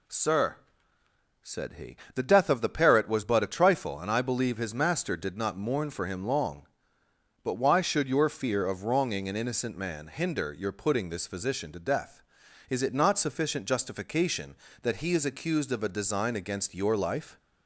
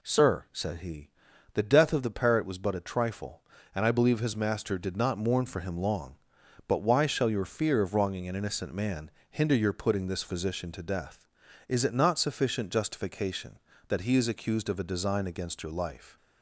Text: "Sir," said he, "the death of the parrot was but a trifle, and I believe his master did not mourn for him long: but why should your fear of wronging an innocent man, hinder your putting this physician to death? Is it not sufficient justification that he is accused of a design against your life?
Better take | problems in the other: first | says "shall" for "should"; at 7.0 s

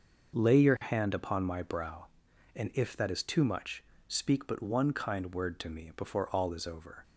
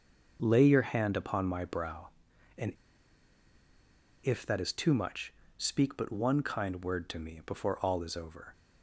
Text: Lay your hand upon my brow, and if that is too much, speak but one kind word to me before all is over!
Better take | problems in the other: first | starts louder than the rest; noticeable; until 1.4 s; 6 dB; noticeable in the first // pauses between "and" and "if"; strong; at 2.7 s; 1.5 s long

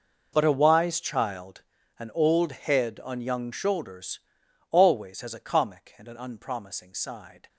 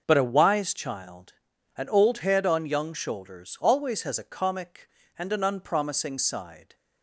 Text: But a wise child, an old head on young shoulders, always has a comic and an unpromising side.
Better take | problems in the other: second | gets quieter; strong; throughout; 17.5 dB

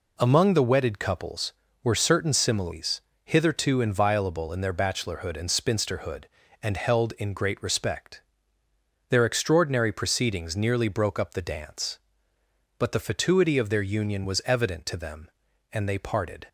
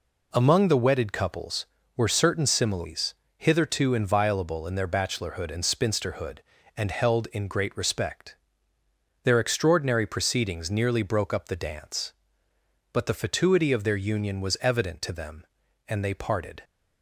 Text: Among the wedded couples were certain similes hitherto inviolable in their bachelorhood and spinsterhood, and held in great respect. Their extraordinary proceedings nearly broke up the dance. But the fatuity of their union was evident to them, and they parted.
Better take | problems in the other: neither | pauses between "similes" and "hitherto"; slight; the same in both

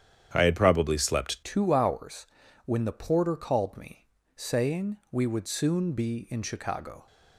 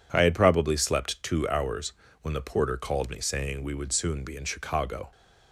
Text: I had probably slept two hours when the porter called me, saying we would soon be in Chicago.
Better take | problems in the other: second | starts louder than the rest; strong; until 1.3 s; 9.5 dB // changes voice at "two"; from 1.4 s on; 5.6 s long // pauses between "hours" and "when"; at 2.2 s; 0.38 s long; slight in the second // pauses between "saying" and "we"; slight; at 4.9 s; 0.16 s long

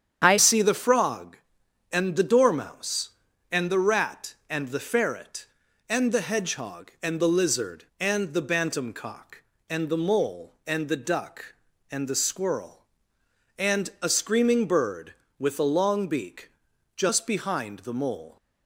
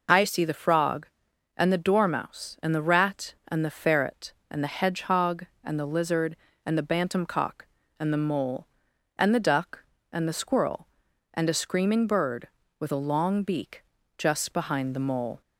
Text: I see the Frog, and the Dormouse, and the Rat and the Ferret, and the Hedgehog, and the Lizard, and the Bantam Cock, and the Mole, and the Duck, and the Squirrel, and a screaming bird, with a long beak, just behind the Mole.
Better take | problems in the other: second | starts louder than the rest; strong; until 1.2 s; 8.5 dB // changes voice at "see"; from 0.3 s on; 18.0 s long

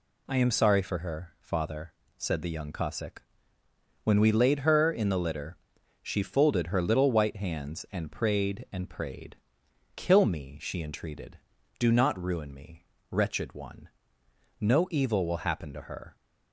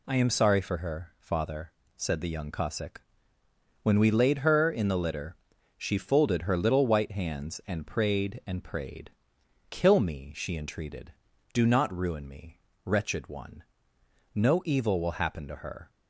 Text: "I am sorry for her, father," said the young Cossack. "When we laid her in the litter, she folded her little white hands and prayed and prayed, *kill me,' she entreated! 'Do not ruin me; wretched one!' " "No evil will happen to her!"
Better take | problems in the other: neither | none

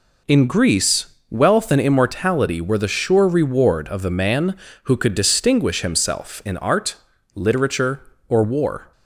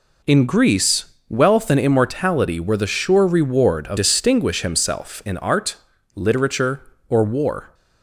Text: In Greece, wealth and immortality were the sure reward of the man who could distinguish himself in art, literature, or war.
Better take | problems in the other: first | skips "the man who could"; at 3.9 s

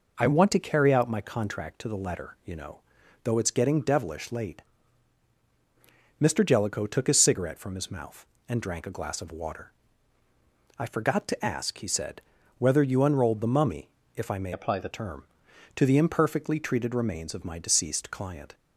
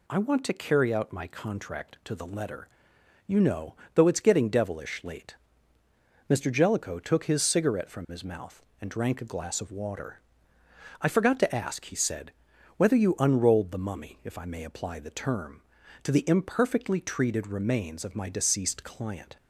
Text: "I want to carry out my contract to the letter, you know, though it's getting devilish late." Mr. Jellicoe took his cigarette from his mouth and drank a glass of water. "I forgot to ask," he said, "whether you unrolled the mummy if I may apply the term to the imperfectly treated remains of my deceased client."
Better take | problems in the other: second | pauses between "mummy" and "if"; slight; at 13.8 s; 0.26 s long // changes voice from "apply" to "the"; from 14.5 to 14.8 s; 0.3 s long

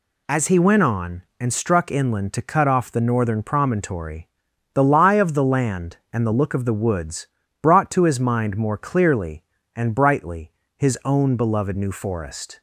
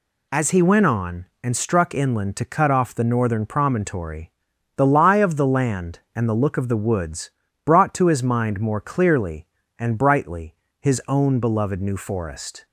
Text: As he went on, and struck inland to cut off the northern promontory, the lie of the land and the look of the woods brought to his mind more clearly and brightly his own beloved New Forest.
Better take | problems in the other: neither | pauses between "woods" and "brought"; slight; the same in both // pauses between "brightly" and "his"; slight; the same in both

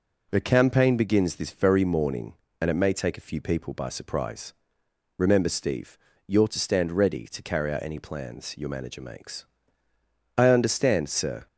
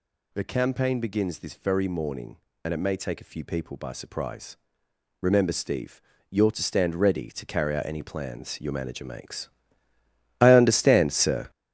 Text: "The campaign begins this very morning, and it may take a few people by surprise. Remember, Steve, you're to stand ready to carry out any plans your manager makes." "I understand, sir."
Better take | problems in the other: first | gets louder; strong; throughout; 8.5 dB

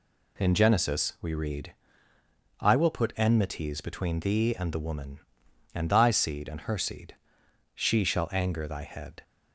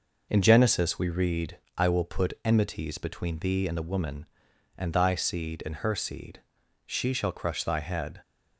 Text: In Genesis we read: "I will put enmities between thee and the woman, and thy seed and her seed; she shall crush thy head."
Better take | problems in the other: second | says "anger" for "crush"; at 8.3 s

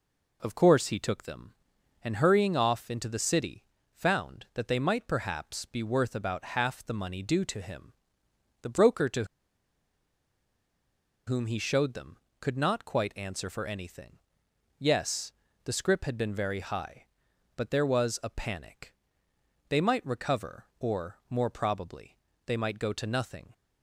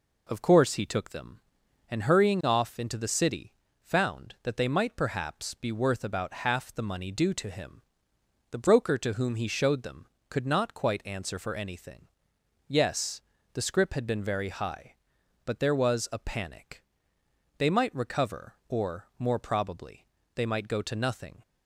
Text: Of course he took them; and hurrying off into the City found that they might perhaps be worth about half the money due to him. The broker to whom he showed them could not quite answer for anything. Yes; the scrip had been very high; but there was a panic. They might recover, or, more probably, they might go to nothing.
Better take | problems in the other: second | pauses between "City" and "found"; slight; at 3.6 s; 0.30 s long; slight in the second // pauses between "to" and "whom"; strong; at 9.2 s; 2.0 s long

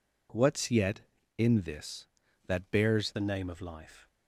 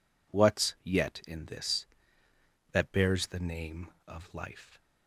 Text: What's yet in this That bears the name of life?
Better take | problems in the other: second | changes voice at "the"; from 3.1 s on; 0.9 s long

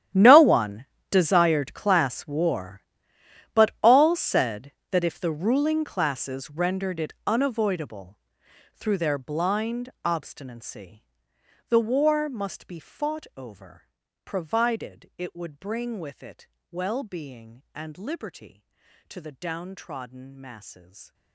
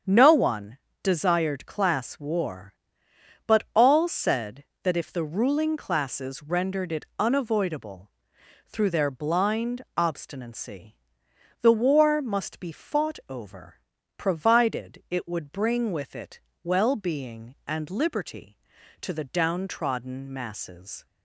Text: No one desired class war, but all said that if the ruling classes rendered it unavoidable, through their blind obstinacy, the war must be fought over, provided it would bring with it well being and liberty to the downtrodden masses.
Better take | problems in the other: second | gets quieter; strong; throughout; 19.5 dB // starts louder than the rest; strong; until 1.4 s; 11 dB; strong in the second // pauses between "one" and "desired"; slight; at 0.8 s; 0.26 s long; slight in the second // pauses between "blind" and "obstinacy"; slight; at 9.8 s; 0.16 s long; slight in the second // pauses between "it" and "well"; slight; at 16.4 s; 0.26 s long; slight in the second

